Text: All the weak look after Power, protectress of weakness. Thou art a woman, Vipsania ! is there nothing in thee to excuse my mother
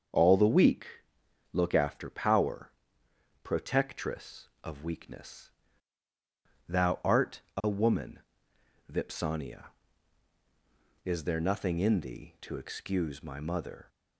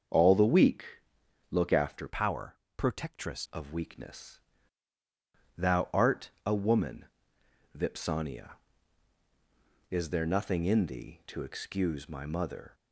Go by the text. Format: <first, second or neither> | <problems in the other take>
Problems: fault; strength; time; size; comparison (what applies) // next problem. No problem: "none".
first | starts louder than the rest; strong; until 1.7 s; 7 dB; strong in the first // pauses between "weak" and "look"; noticeable; at 0.8 s; 0.66 s long; noticeable in the first // changes voice from "Power" to "protectress"; from 2.0 to 3.4 s; 1.4 s long // pauses between "art" and "a"; slight; at 6.2 s; 0.16 s long; slight in the first